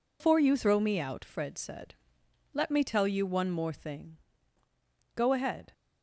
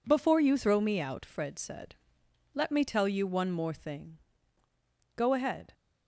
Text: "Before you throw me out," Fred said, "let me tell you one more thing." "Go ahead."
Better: second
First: loses the start of "Before"; at 0.2 s; 145 ms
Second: none

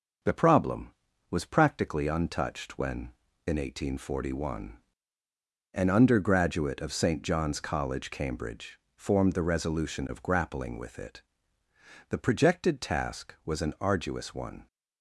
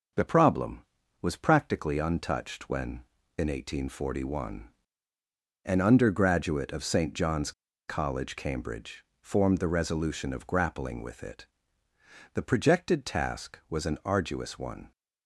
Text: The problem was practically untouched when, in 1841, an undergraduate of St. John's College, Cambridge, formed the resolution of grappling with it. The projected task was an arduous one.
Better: first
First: none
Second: pauses between "John's" and "College"; at 7.5 s; 0.37 s long

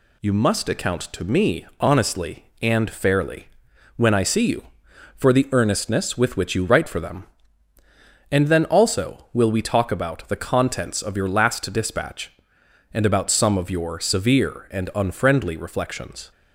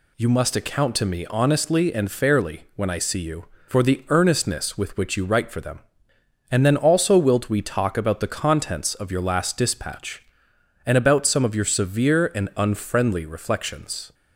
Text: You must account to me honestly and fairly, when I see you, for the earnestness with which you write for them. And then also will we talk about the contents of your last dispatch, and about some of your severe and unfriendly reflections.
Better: first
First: none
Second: says "wilt" for "will"; at 7.1 s

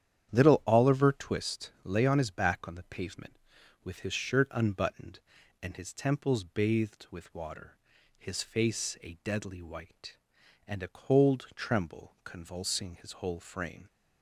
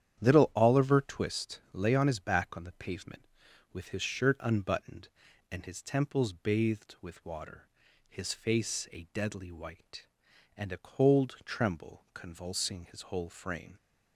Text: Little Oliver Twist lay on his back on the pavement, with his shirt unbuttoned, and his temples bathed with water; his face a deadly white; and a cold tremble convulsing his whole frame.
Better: neither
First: starts louder than the rest; strong; until 1.3 s; 9.5 dB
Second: starts louder than the rest; strong; until 1.2 s; 9.5 dB

